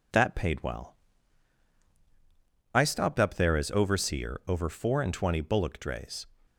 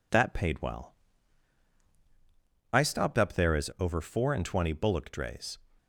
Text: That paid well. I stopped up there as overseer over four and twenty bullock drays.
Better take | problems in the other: first | skips "overseer"; at 3.7 s

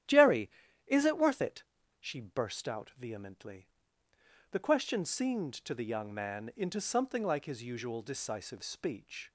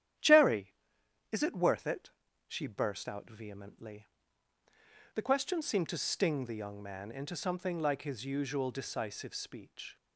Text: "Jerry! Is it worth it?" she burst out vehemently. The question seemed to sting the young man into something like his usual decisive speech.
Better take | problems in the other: second | starts louder than the rest; strong; until 1.4 s; 12 dB; strong in the second // skips "sting"; at 5.7 s

